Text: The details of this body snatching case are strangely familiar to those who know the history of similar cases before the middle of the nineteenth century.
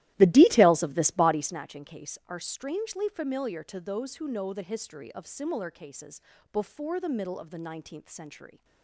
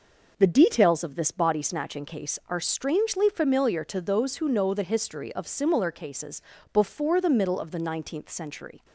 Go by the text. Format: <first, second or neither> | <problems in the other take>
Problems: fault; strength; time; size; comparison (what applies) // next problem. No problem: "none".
second | starts louder than the rest; strong; until 1.6 s; 15.5 dB // pauses between "cases" and "before"; slight; at 6.1 s; 0.32 s long; slight in the second